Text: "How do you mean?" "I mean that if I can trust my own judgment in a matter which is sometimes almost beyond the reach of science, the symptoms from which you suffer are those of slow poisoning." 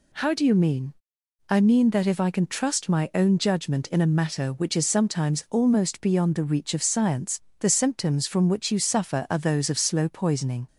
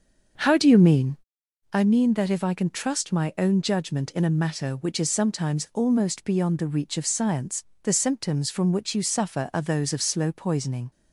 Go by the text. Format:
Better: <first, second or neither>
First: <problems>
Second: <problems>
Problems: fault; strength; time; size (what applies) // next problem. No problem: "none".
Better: first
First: none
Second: starts louder than the rest; until 1.3 s; 6.5 dB